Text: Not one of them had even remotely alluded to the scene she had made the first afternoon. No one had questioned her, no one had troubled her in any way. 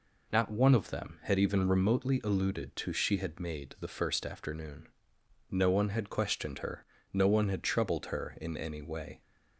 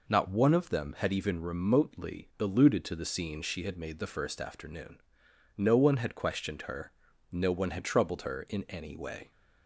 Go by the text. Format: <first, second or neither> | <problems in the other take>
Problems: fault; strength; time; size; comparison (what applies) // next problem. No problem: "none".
second | skips "the scene"; at 2.9 s